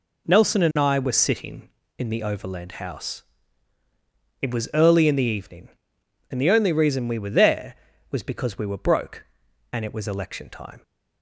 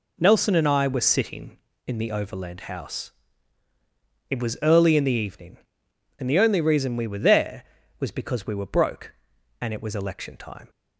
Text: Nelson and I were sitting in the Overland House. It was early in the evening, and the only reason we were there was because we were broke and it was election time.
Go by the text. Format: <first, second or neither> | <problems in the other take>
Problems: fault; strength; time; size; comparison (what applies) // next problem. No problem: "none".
neither | none